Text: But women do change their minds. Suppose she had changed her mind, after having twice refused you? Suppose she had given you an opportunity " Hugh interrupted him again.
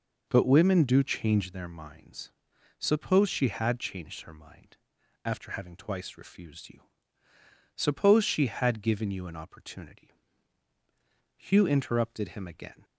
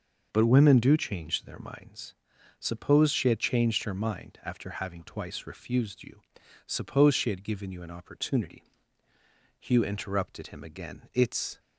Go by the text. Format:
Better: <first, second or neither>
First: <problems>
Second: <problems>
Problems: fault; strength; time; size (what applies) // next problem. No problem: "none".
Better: first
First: none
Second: starts louder than the rest; noticeable; until 1.3 s; 6 dB // goes on to say "It's"; slight; from 11.1 s on; 0.46 s long